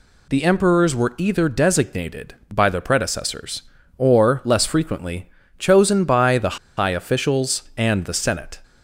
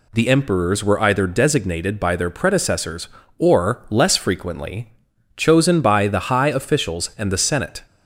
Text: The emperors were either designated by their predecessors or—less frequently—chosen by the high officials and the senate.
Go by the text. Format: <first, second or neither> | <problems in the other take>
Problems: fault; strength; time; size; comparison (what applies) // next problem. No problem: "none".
second | pauses between "the" and "high"; slight; at 6.5 s; 0.21 s long